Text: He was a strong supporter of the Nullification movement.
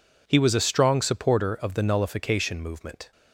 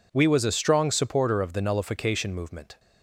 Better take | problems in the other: first | says "We" for "He"; at 0.1 s

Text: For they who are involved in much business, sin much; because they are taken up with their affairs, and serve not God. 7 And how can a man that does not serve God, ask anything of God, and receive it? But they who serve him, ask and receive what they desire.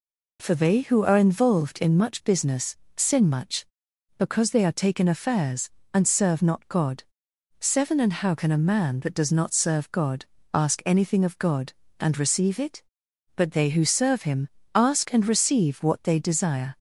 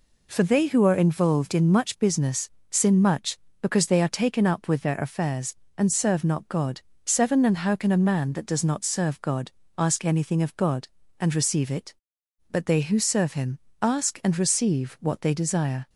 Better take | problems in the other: second | skips "up with their"; at 5.0 s

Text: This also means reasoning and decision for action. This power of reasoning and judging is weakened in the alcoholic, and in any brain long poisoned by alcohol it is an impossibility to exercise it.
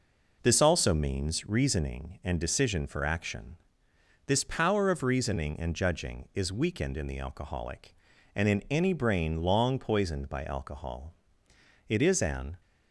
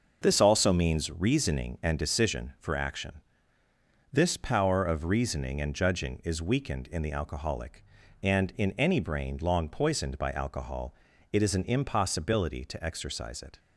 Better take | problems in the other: second | pauses between "alcohol" and "it"; noticeable; at 11.1 s; 0.74 s long; also in the second // stops before "impossibility to exercise it"; at 12.6 s

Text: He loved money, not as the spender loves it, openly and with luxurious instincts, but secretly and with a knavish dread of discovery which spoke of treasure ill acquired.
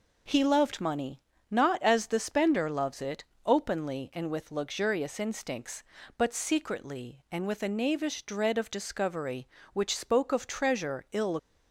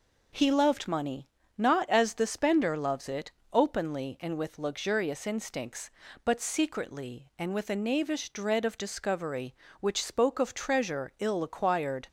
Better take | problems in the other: second | stops before "acquired"; at 11.3 s

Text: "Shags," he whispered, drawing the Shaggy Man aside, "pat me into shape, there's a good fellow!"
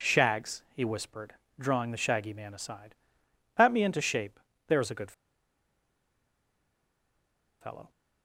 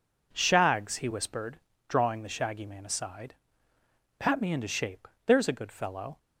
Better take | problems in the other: second | pauses between "good" and "fellow"; strong; at 5.1 s; 2.4 s long

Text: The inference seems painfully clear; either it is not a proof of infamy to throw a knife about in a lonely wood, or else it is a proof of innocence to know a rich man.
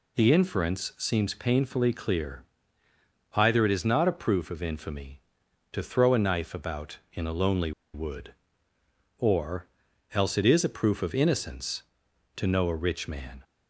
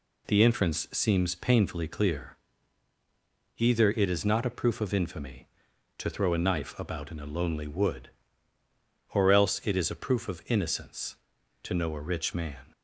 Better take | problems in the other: second | pauses between "lonely" and "wood"; slight; at 7.7 s; 0.23 s long // pauses between "or" and "else"; noticeable; at 9.6 s; 0.46 s long

